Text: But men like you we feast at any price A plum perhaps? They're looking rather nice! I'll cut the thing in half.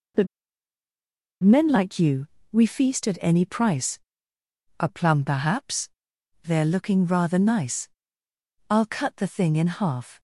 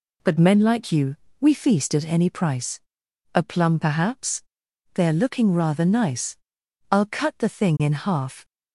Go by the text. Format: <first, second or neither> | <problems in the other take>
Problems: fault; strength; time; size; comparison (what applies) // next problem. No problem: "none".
second | pauses between "But" and "men"; at 0.2 s; 1.1 s long // pauses between "you" and "we"; slight; at 2.2 s; 0.26 s long; slight in the second // pauses between "price" and "A"; noticeable; at 3.9 s; 0.80 s long; noticeable in the second